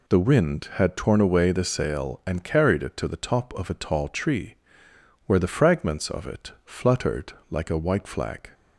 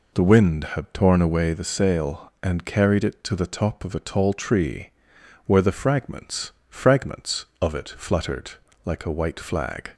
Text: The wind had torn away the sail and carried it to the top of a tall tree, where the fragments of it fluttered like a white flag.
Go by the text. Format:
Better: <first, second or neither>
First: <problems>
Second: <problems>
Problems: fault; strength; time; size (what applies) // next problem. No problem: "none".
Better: first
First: pauses between "fluttered" and "like"; slight; at 7.3 s; 0.16 s long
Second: says "fragments" twice; at 6.6 s // pauses between "fluttered" and "like"; slight; at 8.5 s; 0.34 s long